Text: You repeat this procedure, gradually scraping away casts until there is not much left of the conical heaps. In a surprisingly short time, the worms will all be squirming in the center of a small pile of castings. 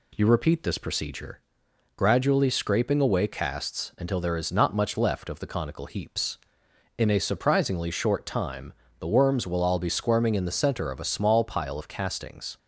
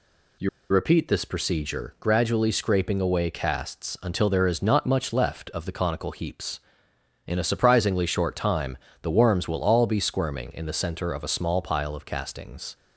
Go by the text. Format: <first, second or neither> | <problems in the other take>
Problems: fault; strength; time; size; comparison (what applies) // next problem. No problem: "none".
first | pauses between "You" and "repeat"; slight; at 0.4 s; 0.23 s long